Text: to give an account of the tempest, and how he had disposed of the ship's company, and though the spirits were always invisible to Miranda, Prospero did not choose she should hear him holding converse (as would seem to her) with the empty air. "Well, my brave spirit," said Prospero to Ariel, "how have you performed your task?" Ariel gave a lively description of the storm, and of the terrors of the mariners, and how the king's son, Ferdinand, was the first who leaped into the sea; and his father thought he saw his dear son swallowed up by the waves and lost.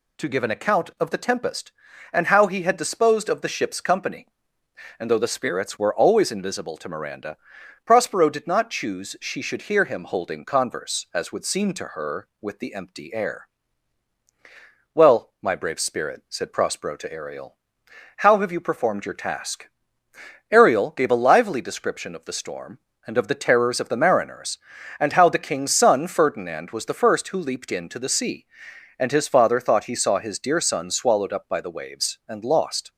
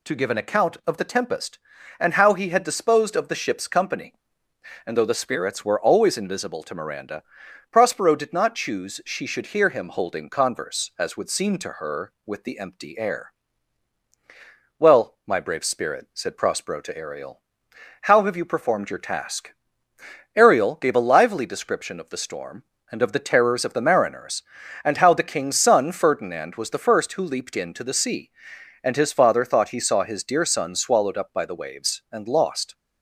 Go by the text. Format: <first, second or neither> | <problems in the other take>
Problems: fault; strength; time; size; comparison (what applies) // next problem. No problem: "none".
neither | none